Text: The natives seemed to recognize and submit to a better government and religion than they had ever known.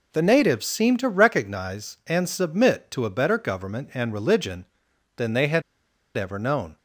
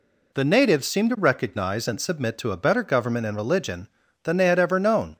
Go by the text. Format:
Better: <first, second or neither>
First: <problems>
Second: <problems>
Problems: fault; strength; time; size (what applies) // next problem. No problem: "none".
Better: second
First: pauses between "had" and "ever"; noticeable; at 5.6 s; 0.54 s long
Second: none